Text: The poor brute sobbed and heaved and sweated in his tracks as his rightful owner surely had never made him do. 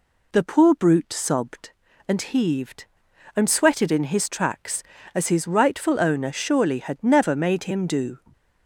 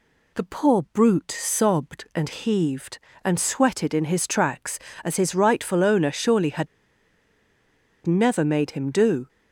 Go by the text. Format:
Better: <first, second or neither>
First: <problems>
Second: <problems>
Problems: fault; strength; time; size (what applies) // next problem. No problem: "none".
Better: first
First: none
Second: pauses between "had" and "never"; strong; at 6.6 s; 1.3 s long